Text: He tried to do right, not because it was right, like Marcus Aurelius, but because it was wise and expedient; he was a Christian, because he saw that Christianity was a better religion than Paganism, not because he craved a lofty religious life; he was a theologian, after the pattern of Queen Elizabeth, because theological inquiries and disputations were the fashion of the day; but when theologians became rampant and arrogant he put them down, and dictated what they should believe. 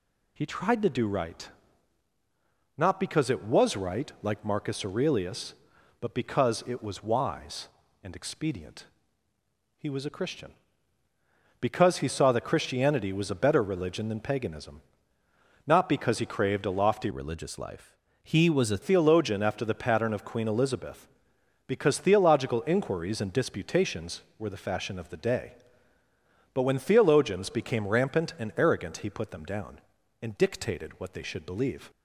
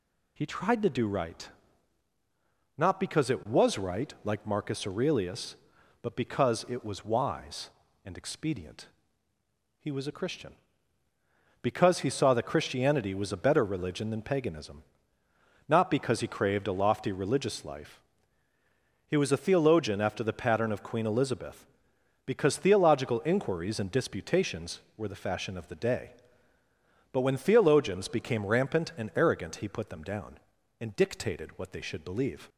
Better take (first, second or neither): second